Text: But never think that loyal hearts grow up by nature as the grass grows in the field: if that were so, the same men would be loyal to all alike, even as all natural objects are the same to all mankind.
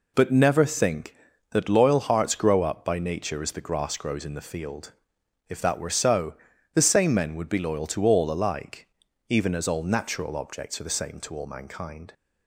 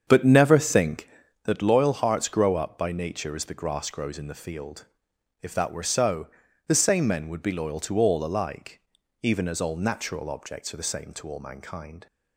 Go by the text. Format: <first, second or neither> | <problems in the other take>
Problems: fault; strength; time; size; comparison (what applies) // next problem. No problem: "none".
first | starts louder than the rest; strong; until 1.4 s; 7.5 dB